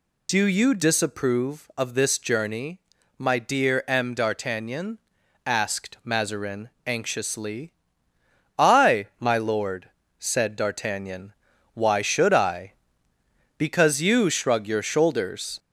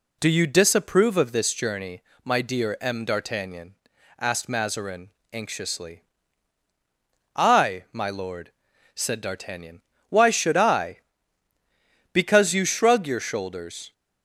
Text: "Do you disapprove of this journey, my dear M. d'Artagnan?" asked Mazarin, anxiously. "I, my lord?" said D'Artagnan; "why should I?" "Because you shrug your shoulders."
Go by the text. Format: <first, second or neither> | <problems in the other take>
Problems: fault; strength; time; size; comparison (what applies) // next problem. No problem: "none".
second | gets louder; slight; throughout; 3 dB